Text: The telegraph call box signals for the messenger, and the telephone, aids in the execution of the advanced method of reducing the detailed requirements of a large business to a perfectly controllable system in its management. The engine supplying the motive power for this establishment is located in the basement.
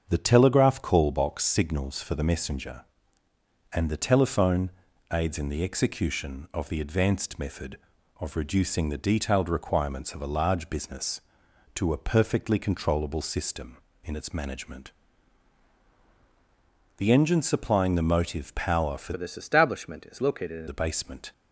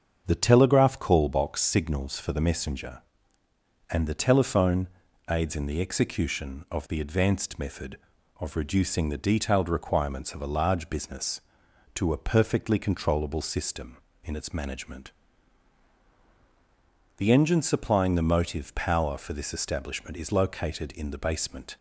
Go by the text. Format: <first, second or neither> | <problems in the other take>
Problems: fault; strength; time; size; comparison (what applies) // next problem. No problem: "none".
second | starts louder than the rest; until 1.1 s; 7 dB; also in the second // changes voice from "this" to "in"; from 19.1 to 20.6 s; 1.5 s long